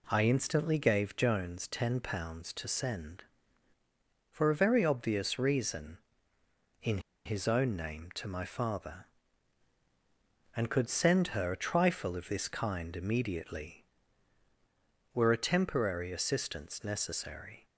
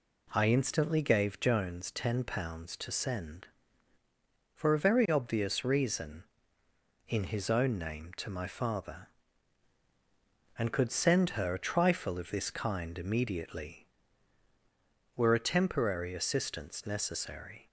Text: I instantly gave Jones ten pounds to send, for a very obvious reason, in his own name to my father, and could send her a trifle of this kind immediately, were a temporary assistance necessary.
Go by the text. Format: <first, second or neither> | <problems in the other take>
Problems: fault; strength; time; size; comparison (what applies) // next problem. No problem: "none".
second | pauses between "in" and "his"; slight; at 6.9 s; 0.26 s long